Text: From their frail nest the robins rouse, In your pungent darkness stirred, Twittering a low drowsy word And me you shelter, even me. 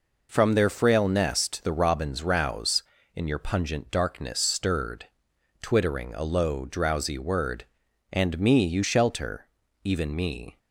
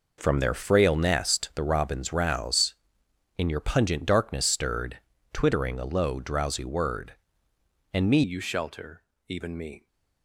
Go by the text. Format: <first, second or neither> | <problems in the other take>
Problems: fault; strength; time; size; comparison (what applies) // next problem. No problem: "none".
first | changes voice at "you"; from 8.2 s on; 1.6 s long